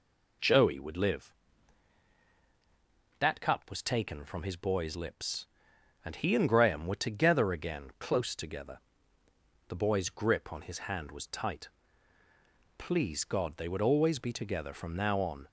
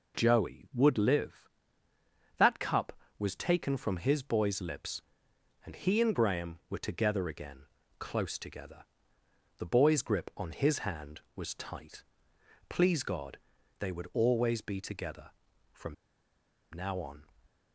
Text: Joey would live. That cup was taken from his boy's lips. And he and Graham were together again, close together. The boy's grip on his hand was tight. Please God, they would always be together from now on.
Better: first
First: none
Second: pauses between "from" and "now"; noticeable; at 15.9 s; 0.77 s long

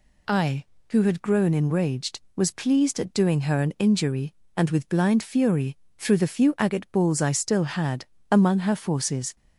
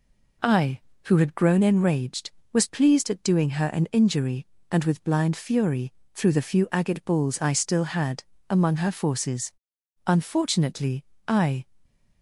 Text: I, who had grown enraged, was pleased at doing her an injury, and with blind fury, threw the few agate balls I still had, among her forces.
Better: first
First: none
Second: goes on to say "Unfortunately I"; from 10.0 s on; 1.5 s long

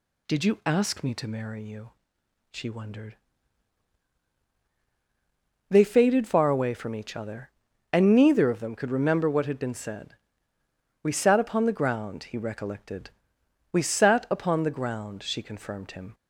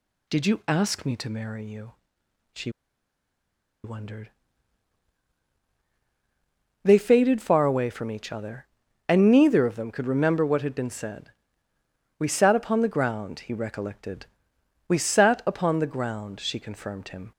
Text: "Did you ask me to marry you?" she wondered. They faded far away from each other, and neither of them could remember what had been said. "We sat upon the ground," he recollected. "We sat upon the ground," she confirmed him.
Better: first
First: none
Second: pauses between "she" and "wondered"; at 2.6 s; 1.1 s long

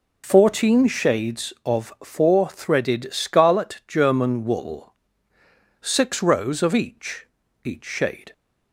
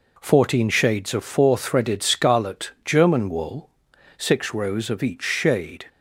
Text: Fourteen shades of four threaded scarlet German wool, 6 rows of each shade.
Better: second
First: says "each" twice; at 7.6 s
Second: none

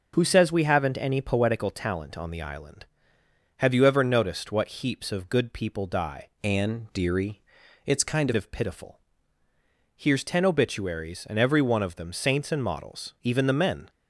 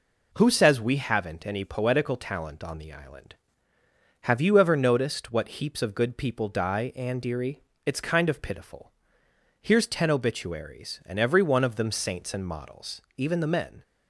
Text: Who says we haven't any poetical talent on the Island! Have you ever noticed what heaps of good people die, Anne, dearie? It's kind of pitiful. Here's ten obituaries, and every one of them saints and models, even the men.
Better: second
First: changes voice from "Anne" to "kind"; from 6.4 to 8.3 s; 1.9 s long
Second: none

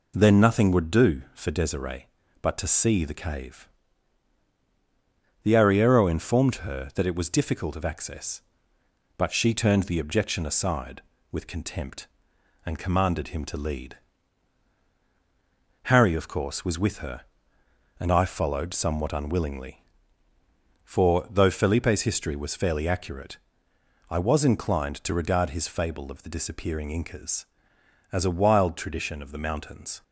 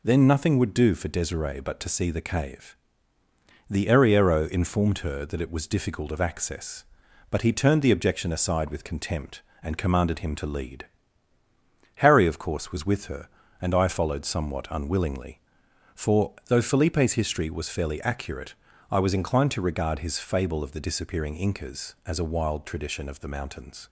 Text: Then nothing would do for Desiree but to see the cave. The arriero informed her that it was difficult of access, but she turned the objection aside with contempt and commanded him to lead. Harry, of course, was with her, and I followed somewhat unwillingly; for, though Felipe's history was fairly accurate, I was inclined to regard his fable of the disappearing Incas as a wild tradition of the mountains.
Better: first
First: none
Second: says "he" for "she"; at 7.4 s

